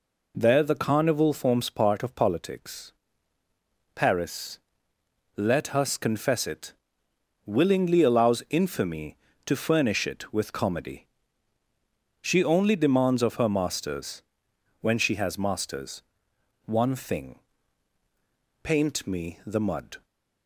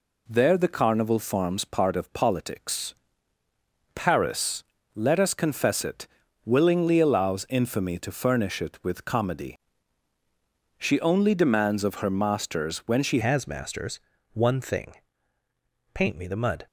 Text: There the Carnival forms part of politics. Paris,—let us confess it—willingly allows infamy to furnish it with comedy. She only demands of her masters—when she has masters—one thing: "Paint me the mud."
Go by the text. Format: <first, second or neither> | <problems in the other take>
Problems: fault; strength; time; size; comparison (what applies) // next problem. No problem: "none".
first | changes voice at "has"; from 13.2 s on; 3.4 s long